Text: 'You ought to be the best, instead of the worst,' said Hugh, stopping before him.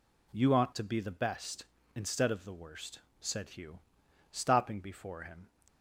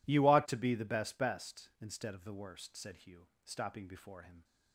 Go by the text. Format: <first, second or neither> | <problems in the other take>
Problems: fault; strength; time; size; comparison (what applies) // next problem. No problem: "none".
first | says "best" twice; at 1.1 s